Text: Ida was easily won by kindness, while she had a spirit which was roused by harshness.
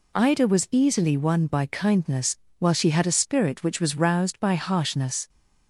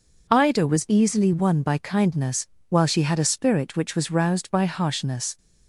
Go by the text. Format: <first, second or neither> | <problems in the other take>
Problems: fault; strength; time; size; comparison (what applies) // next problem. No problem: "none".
neither | none